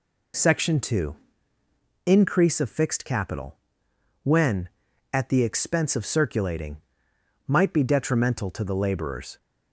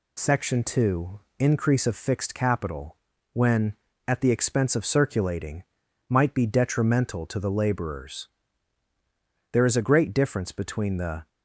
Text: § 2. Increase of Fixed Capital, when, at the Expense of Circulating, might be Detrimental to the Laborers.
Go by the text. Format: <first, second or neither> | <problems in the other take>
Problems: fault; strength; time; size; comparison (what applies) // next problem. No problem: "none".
first | goes on to say "There is a great difference between the"; strong; from 9.5 s on; 1.7 s long